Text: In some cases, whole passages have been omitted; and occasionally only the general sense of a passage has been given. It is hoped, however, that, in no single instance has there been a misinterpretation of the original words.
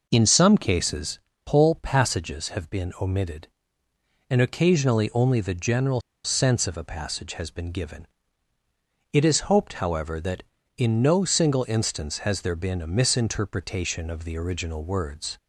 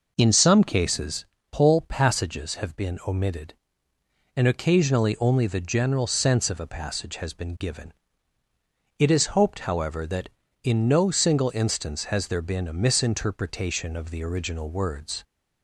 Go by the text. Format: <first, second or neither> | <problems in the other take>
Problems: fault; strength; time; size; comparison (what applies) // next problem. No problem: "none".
second | pauses between "general" and "sense"; slight; at 5.9 s; 0.24 s long